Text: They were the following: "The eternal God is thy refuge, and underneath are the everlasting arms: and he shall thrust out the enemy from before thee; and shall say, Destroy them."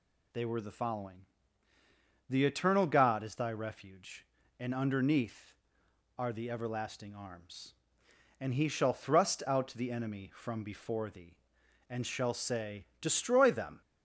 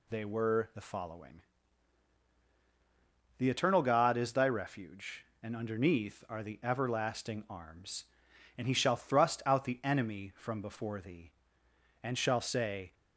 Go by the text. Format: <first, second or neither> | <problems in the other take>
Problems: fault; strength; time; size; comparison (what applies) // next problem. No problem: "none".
first | stops before "Destroy them"; at 12.9 s